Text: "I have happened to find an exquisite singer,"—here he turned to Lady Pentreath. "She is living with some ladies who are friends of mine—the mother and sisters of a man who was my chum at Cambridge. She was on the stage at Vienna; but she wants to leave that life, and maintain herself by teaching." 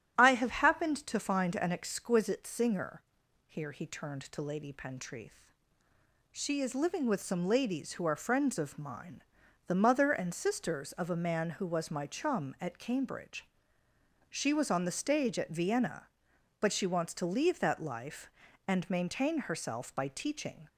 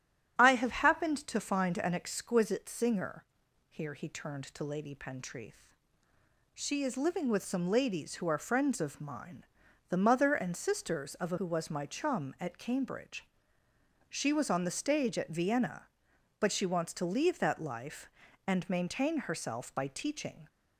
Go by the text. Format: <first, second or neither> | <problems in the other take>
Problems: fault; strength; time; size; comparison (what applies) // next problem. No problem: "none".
first | starts louder than the rest; strong; until 1.4 s; 10 dB; strong in the first // skips "man"; at 11.3 s